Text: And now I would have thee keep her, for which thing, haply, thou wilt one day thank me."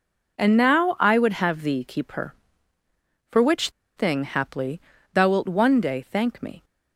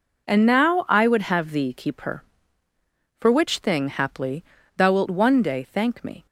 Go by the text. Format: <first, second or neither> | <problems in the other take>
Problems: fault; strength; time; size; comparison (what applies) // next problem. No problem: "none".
second | pauses between "which" and "thing"; slight; at 3.6 s; 0.26 s long